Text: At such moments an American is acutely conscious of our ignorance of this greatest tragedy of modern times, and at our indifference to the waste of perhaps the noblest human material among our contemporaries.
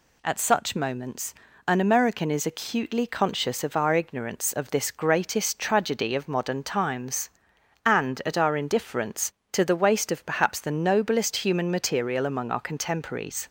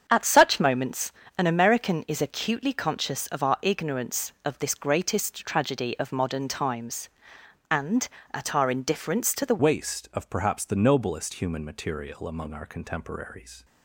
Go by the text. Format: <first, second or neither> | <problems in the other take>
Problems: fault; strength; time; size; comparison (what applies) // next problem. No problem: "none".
first | starts louder than the rest; strong; until 1.0 s; 7.5 dB // pauses between "moments" and "an"; slight; at 1.1 s; 0.26 s long; slight in the first // changes voice at "waste"; from 9.6 s on; 4.0 s long